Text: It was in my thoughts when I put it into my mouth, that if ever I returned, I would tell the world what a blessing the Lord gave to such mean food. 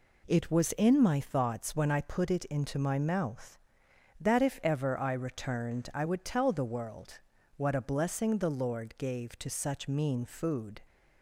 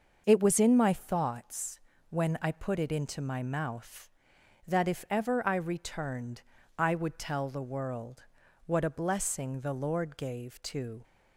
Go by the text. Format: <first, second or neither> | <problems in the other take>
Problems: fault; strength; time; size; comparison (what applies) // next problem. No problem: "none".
first | starts louder than the rest; noticeable; until 1.2 s; 6 dB // pauses between "thoughts" and "when"; slight; at 1.7 s; 0.28 s long // pauses between "world" and "what"; at 8.2 s; 0.42 s long; also in the first // stops before "such mean food"; at 11.0 s